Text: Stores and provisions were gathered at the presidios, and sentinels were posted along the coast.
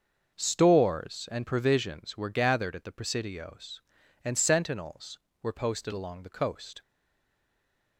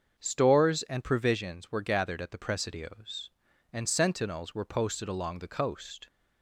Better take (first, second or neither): second